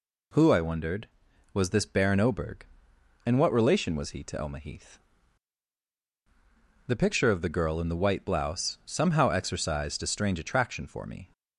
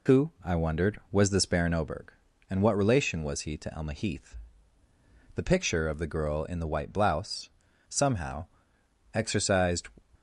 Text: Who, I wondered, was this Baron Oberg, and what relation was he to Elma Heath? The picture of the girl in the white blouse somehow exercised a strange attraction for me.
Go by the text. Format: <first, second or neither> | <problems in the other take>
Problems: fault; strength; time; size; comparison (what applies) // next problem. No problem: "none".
first | pauses between "blouse" and "somehow"; at 7.4 s; 0.40 s long // pauses between "somehow" and "exercised"; noticeable; at 8.4 s; 0.68 s long // stops before "a strange attraction for me"; at 10.1 s